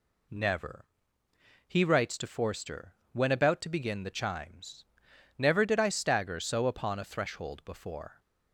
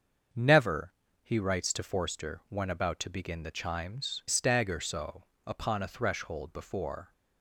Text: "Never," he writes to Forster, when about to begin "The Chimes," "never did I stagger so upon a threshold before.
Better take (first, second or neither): first